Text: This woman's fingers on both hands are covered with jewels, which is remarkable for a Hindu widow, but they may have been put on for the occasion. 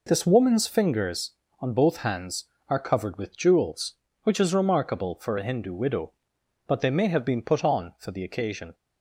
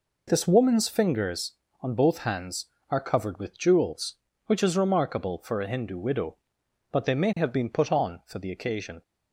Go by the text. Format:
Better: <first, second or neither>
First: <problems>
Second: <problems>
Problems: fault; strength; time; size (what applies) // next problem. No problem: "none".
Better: neither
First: none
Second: none